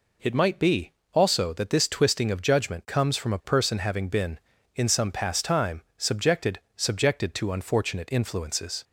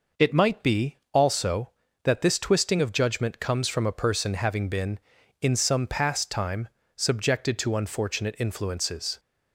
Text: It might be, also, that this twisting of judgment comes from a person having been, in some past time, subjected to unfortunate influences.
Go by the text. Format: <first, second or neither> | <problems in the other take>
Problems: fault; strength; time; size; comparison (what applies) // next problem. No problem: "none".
second | says "subjected" twice; at 6.7 s